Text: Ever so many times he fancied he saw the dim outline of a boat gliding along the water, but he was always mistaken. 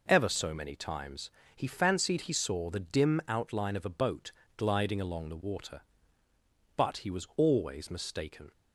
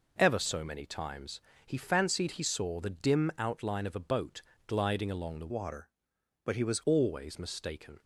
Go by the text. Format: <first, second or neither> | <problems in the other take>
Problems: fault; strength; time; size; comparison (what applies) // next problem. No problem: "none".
first | pauses between "times" and "he"; slight; at 1.4 s; 0.22 s long; slight in the first // pauses between "boat" and "gliding"; slight; at 4.4 s; 0.24 s long; slight in the first // changes voice from "water" to "was"; from 5.4 to 6.8 s; 1.4 s long